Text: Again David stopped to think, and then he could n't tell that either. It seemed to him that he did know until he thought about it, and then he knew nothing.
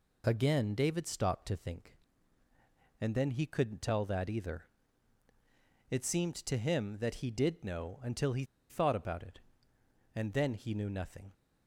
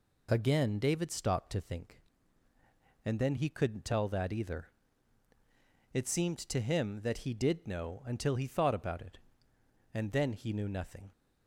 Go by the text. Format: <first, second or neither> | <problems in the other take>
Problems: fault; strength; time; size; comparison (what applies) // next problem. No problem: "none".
second | pauses between "he" and "thought"; slight; at 8.4 s; 0.26 s long